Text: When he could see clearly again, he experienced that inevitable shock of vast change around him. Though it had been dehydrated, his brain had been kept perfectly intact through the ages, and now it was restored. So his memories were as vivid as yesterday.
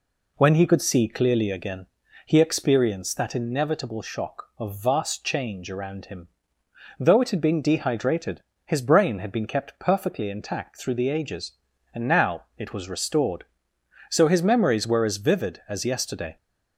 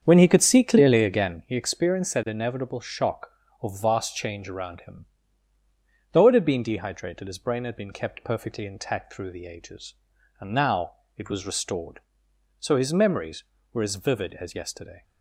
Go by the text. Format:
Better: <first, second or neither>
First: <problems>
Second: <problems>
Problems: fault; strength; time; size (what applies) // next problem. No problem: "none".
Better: first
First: none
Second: starts louder than the rest; strong; until 1.6 s; 8 dB // pauses between "now" and "it"; slight; at 10.9 s; 0.24 s long